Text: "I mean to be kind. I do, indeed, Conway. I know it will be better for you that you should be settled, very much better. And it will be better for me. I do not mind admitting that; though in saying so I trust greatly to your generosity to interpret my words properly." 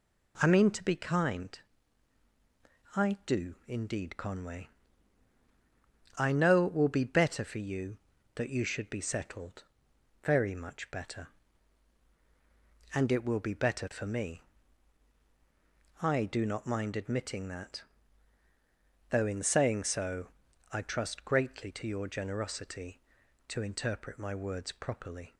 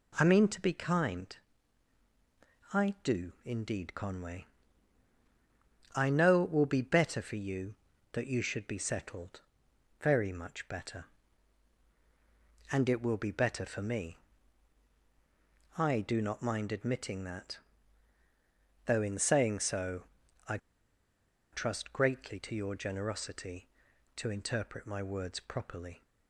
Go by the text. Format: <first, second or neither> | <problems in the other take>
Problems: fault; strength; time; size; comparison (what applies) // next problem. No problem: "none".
first | pauses between "so" and "I"; at 20.0 s; 0.44 s long; also in the first // pauses between "I" and "trust"; noticeable; at 20.5 s; 0.95 s long